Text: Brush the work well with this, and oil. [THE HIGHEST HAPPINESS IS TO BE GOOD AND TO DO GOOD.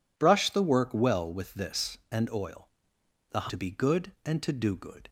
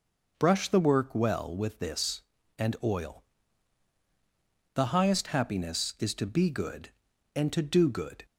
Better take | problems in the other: second | skips "HIGHEST HAPPINESS IS"; at 3.4 s

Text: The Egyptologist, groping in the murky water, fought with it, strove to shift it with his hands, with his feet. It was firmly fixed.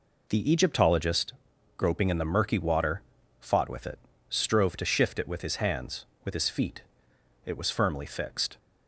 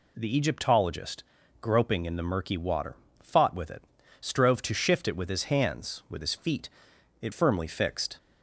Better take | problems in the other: first | skips "was"; at 7.3 s

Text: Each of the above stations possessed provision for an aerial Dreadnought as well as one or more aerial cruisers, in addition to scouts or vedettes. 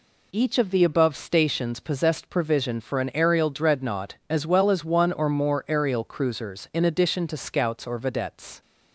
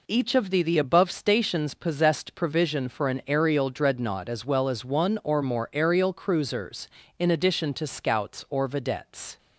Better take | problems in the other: first | says "the" twice; at 0.6 s

